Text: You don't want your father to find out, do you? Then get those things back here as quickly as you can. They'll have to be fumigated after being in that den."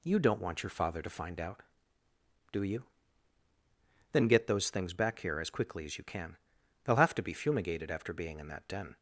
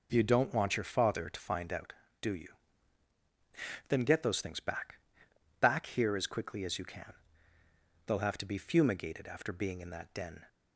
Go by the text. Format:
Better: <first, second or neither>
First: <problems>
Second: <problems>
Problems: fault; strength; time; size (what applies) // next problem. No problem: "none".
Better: first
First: none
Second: says "back" twice; at 5.5 s